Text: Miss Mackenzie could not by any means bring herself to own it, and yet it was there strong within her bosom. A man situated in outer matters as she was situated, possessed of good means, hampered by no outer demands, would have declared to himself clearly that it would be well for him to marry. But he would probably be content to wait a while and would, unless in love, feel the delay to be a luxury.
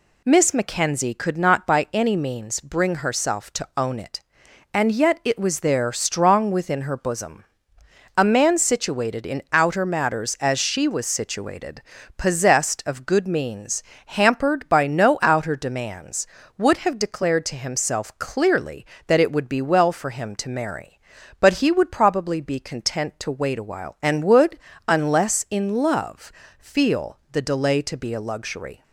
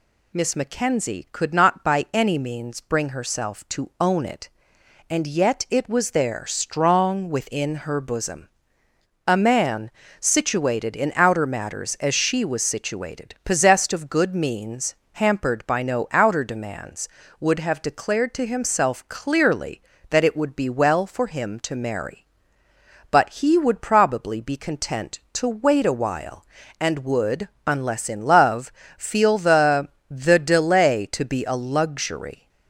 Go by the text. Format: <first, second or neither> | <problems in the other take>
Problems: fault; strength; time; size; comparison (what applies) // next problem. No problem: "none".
first | pauses between "man" and "situated"; slight; at 9.9 s; 0.30 s long // says "the" twice; at 30.1 s